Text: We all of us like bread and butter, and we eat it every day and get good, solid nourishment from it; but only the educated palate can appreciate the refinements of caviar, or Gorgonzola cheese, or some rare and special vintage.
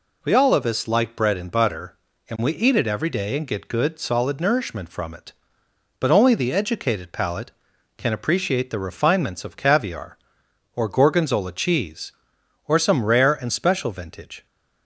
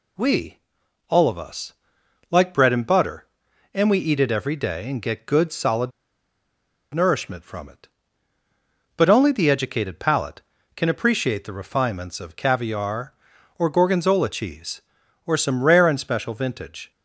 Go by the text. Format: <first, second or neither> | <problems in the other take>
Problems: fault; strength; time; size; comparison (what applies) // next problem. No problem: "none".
first | pauses between "We" and "all"; noticeable; at 0.5 s; 0.50 s long // pauses between "us" and "like"; noticeable; at 1.7 s; 0.56 s long // pauses between "solid" and "nourishment"; at 5.9 s; 1.0 s long